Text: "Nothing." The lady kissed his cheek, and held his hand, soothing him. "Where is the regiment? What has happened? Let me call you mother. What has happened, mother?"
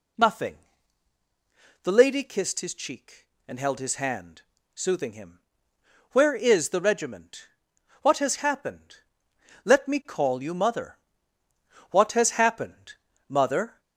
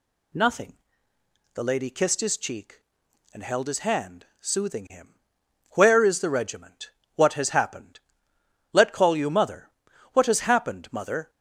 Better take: first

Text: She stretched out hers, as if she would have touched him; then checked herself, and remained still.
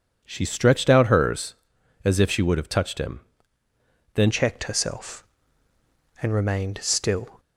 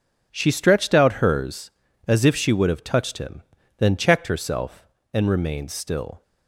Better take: second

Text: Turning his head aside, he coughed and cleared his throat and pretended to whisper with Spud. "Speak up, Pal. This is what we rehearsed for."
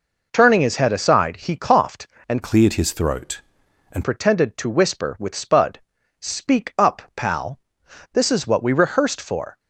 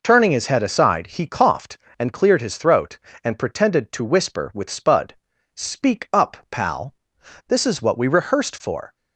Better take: second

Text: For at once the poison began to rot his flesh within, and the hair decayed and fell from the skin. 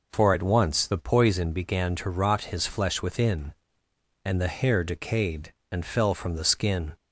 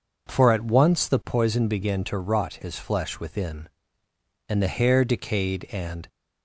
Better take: first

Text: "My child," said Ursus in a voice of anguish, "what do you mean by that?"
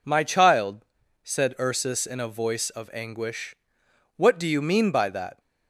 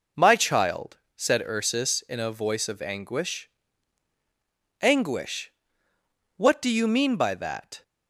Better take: first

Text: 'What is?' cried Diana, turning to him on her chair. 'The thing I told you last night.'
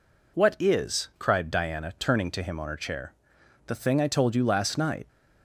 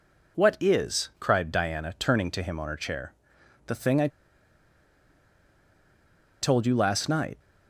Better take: first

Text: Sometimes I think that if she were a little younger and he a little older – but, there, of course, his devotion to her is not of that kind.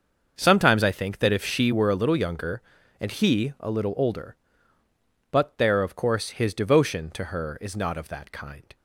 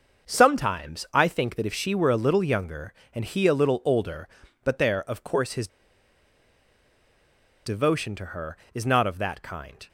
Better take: first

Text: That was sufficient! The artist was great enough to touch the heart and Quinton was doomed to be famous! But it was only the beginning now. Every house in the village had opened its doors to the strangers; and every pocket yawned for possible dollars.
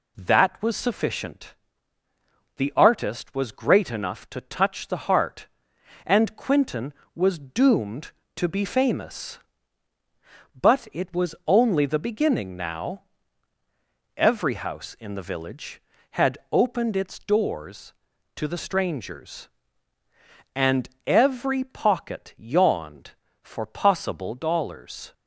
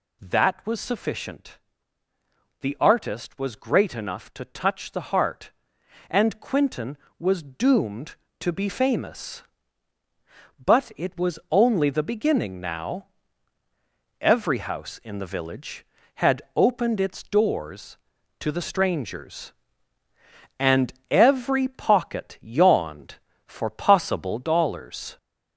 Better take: first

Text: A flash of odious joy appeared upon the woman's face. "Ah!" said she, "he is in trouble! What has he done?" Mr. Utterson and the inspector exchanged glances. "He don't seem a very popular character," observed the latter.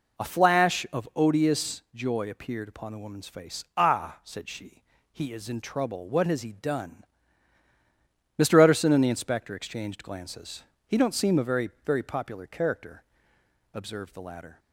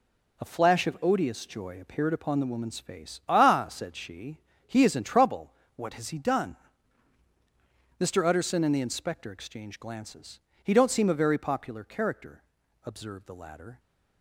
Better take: second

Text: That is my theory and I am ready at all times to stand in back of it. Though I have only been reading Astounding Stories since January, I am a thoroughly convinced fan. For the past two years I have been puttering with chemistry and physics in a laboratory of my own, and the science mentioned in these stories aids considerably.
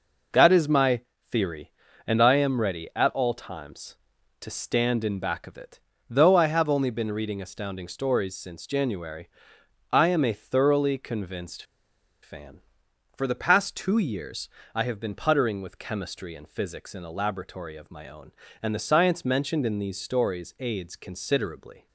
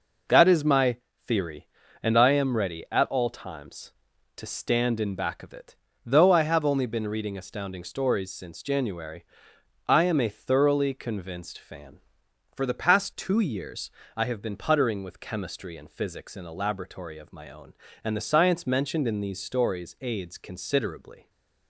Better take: second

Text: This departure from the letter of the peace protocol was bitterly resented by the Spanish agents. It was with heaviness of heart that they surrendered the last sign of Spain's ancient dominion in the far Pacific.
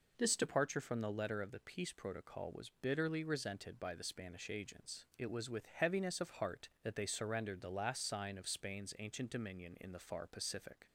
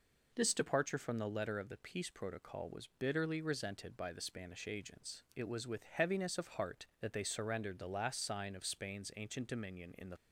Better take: first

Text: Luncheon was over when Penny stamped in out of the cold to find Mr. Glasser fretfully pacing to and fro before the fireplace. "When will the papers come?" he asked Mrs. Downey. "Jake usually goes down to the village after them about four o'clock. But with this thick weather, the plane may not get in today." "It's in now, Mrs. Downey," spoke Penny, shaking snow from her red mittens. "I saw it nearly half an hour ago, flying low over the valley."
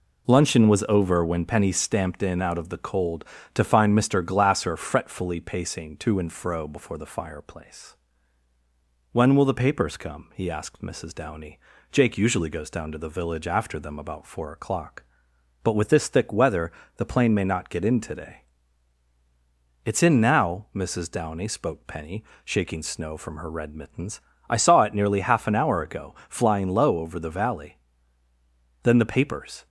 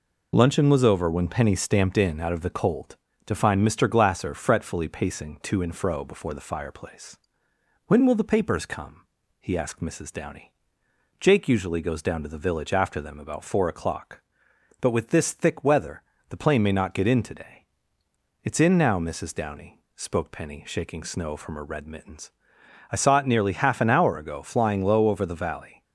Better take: second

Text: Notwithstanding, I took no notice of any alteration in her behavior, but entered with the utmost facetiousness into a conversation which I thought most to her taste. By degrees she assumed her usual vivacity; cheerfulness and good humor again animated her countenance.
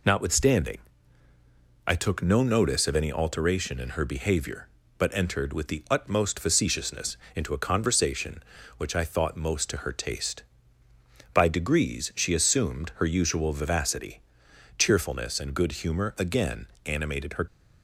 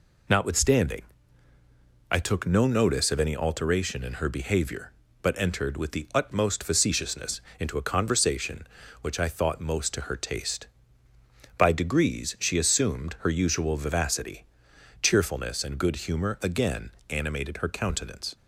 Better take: second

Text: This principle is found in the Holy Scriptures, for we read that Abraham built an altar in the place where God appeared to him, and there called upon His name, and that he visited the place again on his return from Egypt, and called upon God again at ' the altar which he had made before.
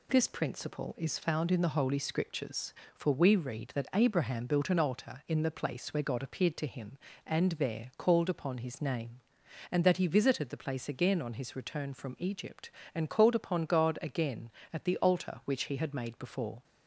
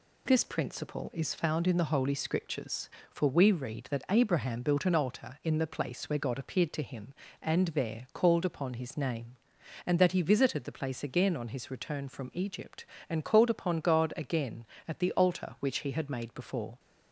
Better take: neither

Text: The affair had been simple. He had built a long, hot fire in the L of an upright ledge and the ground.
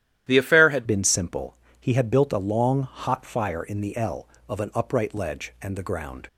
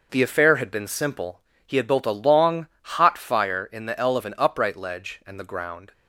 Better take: second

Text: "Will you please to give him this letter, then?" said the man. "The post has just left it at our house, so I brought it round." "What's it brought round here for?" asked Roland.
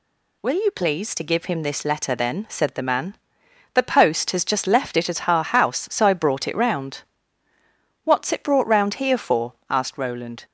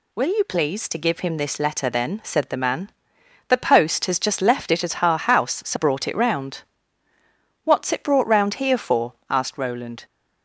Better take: first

